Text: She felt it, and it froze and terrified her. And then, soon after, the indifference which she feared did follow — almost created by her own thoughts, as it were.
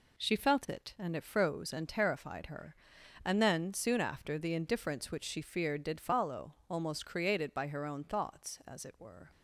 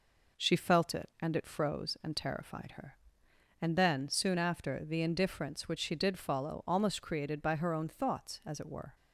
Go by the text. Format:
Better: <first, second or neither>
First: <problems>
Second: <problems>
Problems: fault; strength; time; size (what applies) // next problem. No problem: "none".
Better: first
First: none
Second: skips "feared"; at 5.9 s